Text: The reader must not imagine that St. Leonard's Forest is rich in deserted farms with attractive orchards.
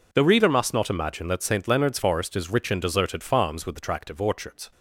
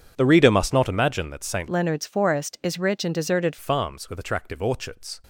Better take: first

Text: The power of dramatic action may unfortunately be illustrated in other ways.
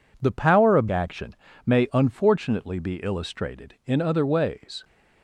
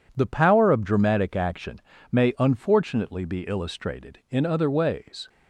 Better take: second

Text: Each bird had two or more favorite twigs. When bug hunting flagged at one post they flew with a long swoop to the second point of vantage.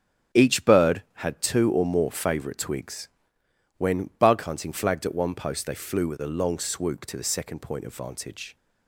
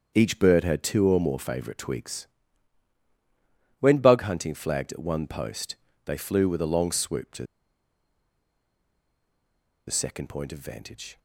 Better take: first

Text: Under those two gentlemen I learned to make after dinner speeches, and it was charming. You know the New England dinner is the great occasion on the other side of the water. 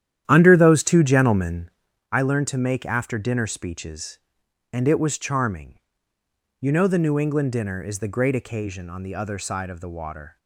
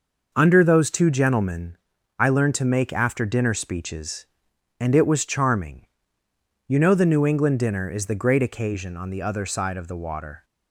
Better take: second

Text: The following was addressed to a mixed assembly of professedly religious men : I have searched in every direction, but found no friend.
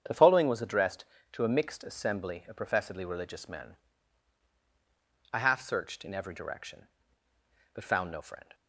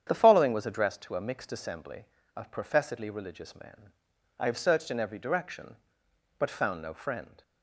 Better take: second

